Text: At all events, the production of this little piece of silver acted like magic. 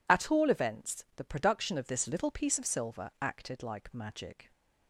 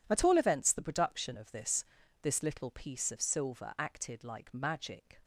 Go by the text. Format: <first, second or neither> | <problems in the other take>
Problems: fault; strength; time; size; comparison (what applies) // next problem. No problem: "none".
first | says "this" twice; at 2.2 s